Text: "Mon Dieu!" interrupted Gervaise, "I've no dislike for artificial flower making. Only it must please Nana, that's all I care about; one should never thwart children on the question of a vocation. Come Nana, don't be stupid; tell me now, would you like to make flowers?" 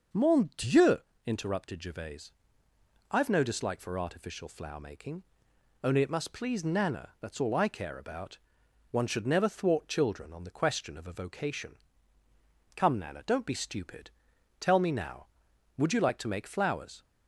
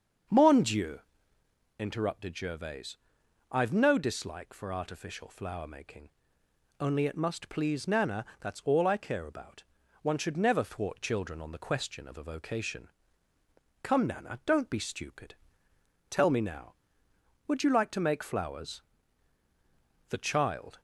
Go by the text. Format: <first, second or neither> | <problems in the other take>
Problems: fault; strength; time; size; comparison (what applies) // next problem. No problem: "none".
first | starts louder than the rest; until 2.0 s; 7 dB; noticeable in the first // goes on to say "The child"; noticeable; from 20.0 s on; 0.72 s long